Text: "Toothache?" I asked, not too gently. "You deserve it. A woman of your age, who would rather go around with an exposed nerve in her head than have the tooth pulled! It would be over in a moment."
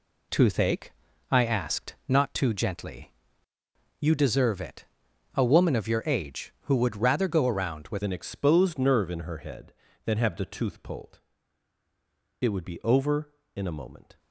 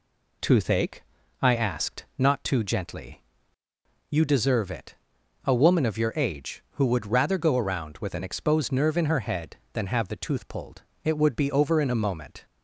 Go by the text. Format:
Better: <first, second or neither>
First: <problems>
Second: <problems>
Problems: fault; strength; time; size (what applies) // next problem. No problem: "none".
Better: second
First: changes voice at "an"; from 8.0 s on; 6.1 s long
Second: none